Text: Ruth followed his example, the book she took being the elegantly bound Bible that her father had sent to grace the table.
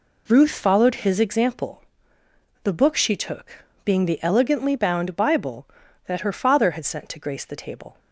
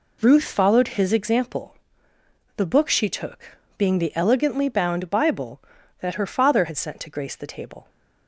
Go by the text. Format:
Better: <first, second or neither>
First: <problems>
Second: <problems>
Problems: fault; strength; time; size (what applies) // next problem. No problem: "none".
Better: neither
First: pauses between "took" and "being"; slight; at 3.6 s; 0.20 s long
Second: pauses between "took" and "being"; slight; at 3.5 s; 0.20 s long